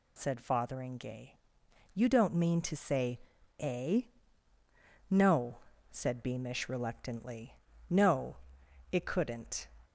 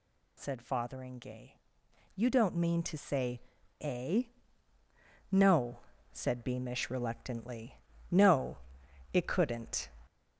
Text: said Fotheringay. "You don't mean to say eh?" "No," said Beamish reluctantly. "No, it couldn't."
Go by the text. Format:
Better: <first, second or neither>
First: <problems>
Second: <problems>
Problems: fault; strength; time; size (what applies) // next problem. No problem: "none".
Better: first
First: pauses between "say" and "eh"; at 3.1 s; 0.40 s long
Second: gets louder; throughout; 3.5 dB // pauses between "say" and "eh"; at 3.4 s; 0.40 s long